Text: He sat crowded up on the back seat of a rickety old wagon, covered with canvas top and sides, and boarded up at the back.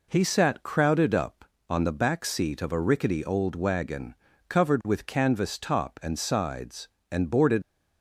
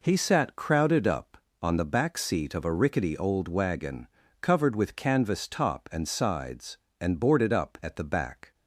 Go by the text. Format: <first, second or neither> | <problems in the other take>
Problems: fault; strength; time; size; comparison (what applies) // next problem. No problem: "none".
second | stops before "up at the back"; at 7.6 s